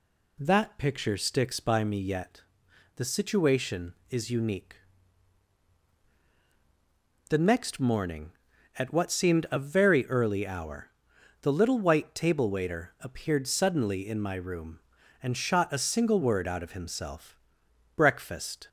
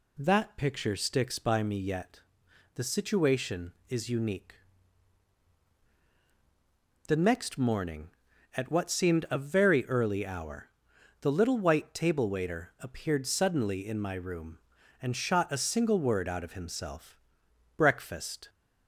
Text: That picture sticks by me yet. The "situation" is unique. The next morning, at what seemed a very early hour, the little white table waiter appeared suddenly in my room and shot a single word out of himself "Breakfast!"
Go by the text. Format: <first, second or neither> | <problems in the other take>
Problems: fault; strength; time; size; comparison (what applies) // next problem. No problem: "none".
neither | pauses between "himself" and "Breakfast"; noticeable; the same in both